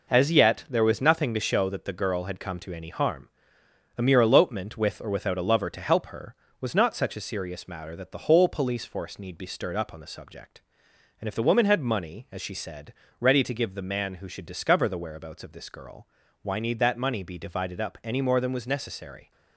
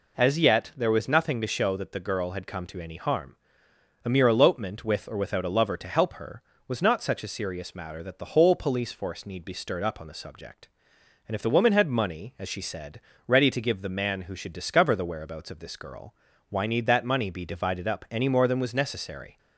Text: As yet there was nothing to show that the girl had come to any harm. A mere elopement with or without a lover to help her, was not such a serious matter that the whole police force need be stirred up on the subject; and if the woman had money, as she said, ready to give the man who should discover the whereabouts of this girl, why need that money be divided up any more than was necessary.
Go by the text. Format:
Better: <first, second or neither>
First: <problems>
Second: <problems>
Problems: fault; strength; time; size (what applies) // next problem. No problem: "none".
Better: second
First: gets quieter; throughout; 6.5 dB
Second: none